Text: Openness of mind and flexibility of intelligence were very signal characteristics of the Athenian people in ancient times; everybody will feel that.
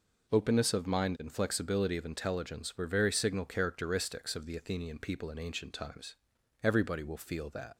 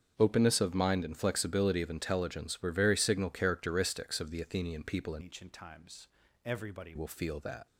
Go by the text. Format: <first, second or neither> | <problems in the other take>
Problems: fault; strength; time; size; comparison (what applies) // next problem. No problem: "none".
first | starts louder than the rest; strong; until 1.1 s; 7.5 dB // changes voice from "ancient" to "everybody"; from 5.2 to 6.9 s; 1.7 s long